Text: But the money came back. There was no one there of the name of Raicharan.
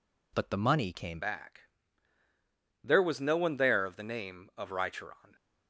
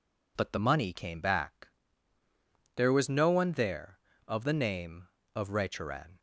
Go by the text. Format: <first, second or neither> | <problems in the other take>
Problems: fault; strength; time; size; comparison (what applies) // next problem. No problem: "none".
second | changes voice at "back"; from 1.1 s on; 4.2 s long